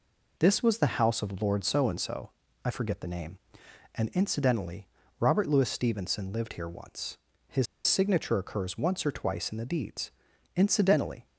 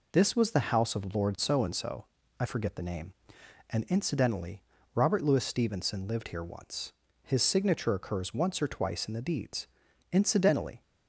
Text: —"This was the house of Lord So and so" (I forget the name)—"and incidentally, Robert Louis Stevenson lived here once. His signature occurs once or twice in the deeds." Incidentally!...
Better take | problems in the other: second | pauses between "His" and "signature"; slight; at 7.6 s; 0.21 s long

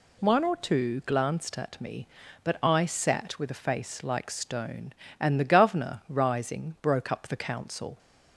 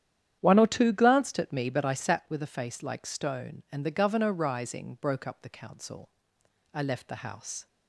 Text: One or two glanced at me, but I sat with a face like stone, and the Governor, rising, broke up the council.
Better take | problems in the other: first | starts louder than the rest; strong; until 1.4 s; 10 dB // goes on to say "I left the house"; noticeable; from 6.7 s on; 0.94 s long

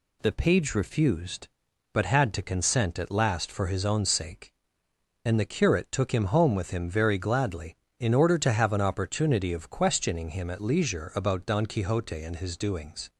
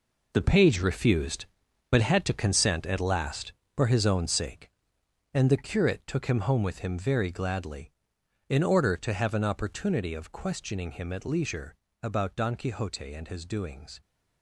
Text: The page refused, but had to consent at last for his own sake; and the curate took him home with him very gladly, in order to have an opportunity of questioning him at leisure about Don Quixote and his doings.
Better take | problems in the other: first | gets quieter; strong; throughout; 11 dB // pauses between "leisure" and "about"; slight; at 11.7 s; 0.28 s long

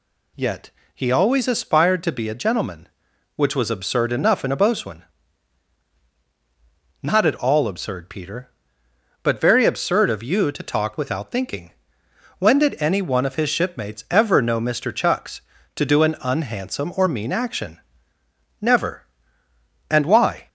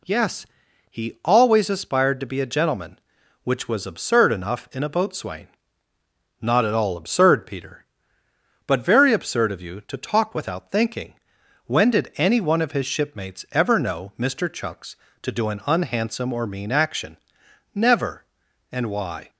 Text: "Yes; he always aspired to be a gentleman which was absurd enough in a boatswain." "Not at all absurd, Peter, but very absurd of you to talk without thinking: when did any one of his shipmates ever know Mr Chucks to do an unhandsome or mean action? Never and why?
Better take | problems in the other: second | says "Yet" for "Yes"; at 0.3 s

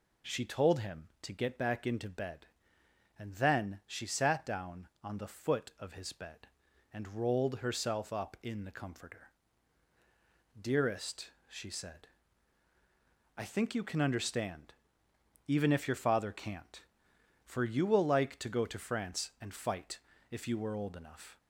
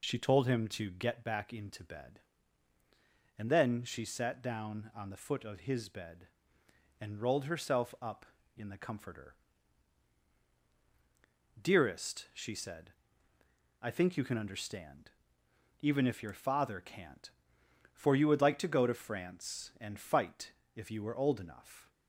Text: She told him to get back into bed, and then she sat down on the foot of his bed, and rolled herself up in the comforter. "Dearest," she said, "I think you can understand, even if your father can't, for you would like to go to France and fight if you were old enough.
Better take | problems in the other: second | says "will" for "would"; at 17.8 s // pauses between "fight" and "if"; slight; at 19.9 s; 0.32 s long; slight in the second

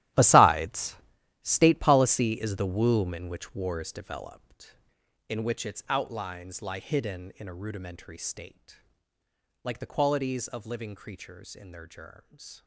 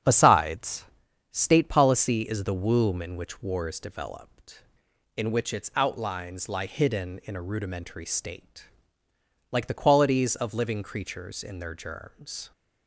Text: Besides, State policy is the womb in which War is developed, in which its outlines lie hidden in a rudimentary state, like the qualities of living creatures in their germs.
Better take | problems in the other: second | gets quieter; strong; throughout; 15.5 dB // starts louder than the rest; strong; until 1.6 s; 13.5 dB; strong in the second

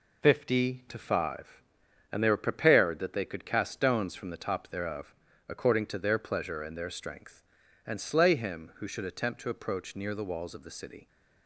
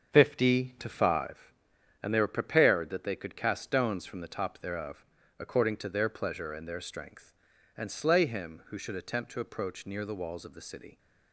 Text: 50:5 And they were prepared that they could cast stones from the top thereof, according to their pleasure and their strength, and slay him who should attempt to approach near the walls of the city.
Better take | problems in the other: first | starts louder than the rest; until 1.4 s; 7 dB

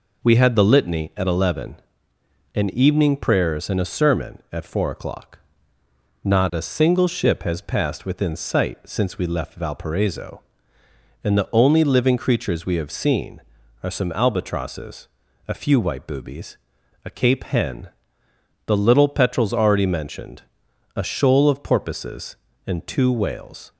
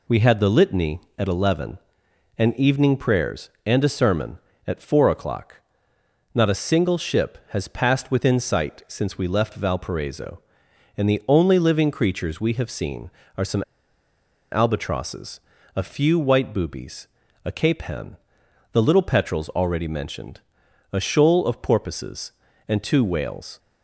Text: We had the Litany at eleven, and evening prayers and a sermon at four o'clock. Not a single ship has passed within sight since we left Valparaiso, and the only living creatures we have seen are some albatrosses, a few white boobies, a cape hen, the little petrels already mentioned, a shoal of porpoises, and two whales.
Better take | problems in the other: first | pauses between "some" and "albatrosses"; noticeable; at 13.6 s; 0.87 s long

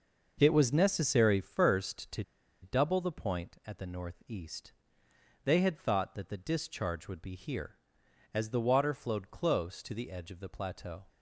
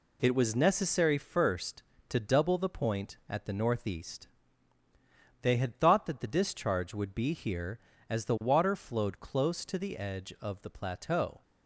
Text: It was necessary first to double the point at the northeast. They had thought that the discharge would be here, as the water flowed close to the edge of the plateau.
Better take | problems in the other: second | pauses between "to" and "double"; at 2.2 s; 0.39 s long

